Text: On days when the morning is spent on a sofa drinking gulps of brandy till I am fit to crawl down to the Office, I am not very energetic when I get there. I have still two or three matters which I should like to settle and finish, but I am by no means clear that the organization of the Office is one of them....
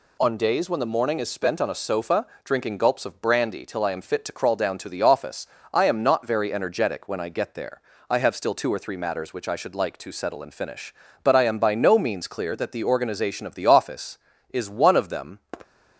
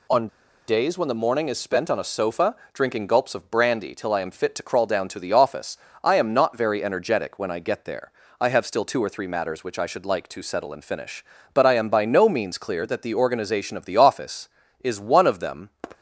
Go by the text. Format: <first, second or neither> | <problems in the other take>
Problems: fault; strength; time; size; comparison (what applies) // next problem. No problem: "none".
first | pauses between "On" and "days"; at 0.2 s; 0.40 s long // pauses between "sofa" and "drinking"; slight; at 2.5 s; 0.16 s long; slight in the first